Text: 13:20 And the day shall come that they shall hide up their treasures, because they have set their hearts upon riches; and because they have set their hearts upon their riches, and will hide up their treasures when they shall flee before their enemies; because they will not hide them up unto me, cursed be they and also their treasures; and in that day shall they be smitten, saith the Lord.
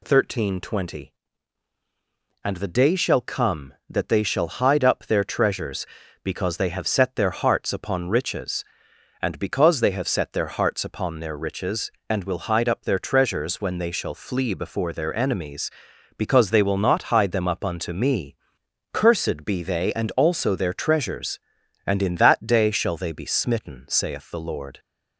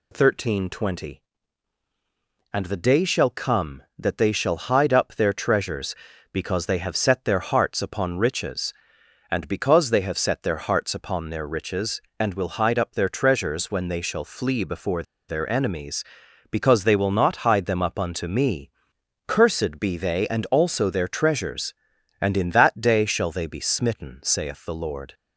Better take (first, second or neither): first